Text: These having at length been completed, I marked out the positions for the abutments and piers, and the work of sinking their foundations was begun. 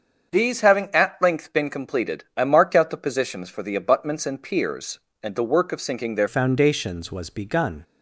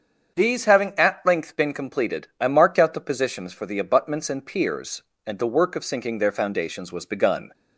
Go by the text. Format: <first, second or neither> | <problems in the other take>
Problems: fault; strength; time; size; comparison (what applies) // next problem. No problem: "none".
second | starts louder than the rest; until 1.3 s; 7 dB; strong in the second // changes voice at "foundations"; from 6.2 s on; 1.6 s long